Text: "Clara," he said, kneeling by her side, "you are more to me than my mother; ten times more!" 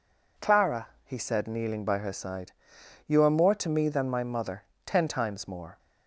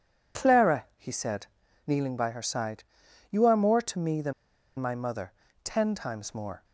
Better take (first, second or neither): first